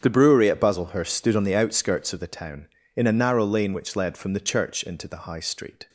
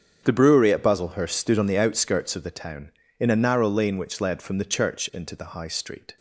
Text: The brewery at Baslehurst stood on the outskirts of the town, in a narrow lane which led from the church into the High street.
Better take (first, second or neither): neither